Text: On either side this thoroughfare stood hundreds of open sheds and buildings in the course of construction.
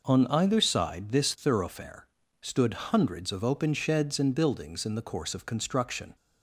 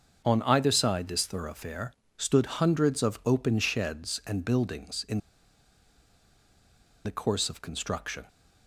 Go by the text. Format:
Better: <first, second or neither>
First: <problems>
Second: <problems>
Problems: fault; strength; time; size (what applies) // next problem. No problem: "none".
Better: first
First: pauses between "thoroughfare" and "stood"; slight; at 2.0 s; 0.34 s long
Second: starts louder than the rest; until 1.2 s; 6.5 dB // pauses between "thoroughfare" and "stood"; slight; at 1.9 s; 0.24 s long // pauses between "in" and "the"; strong; at 5.1 s; 1.8 s long